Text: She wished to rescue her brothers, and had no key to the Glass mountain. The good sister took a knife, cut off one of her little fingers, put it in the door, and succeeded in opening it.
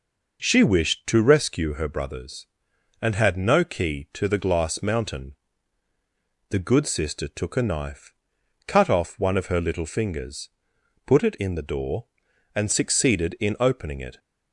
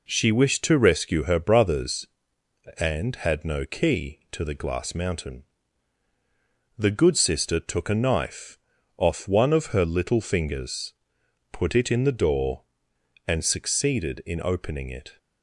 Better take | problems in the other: first | skips "cut"; at 8.7 s

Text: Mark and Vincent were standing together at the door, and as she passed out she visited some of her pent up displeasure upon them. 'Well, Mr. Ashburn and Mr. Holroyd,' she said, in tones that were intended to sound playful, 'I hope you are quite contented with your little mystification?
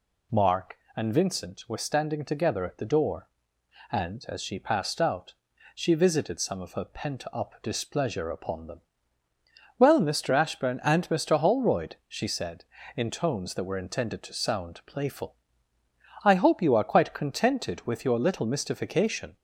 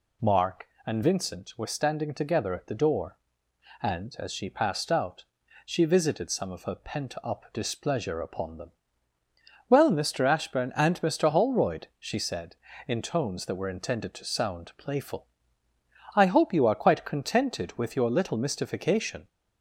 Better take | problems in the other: neither | pauses between "out" and "she"; the same in both

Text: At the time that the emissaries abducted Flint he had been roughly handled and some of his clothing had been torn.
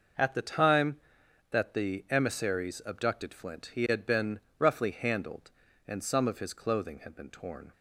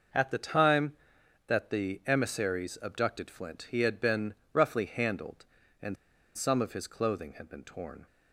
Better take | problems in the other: first | pauses between "been" and "roughly"; slight; at 4.3 s; 0.18 s long; slight in the first // pauses between "and" and "some"; at 5.9 s; 0.39 s long

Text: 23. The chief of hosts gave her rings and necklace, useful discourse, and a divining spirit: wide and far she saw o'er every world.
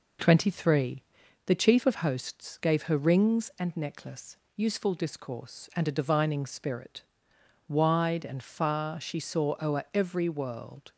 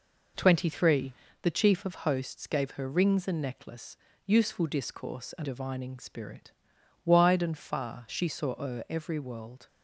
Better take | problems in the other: first | skips "a"; at 5.4 s

